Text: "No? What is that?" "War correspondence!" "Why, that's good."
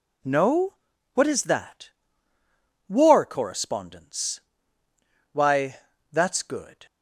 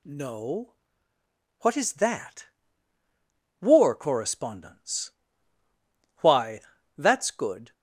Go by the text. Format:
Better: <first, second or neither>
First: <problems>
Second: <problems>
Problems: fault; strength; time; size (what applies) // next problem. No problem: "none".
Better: neither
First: none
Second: none